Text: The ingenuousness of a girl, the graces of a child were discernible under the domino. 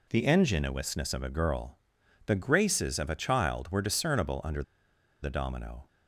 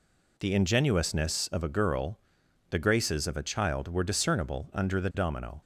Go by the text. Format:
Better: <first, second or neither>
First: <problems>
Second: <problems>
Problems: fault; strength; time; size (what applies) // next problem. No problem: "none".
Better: second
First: pauses between "under" and "the"; noticeable; at 4.6 s; 0.60 s long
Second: none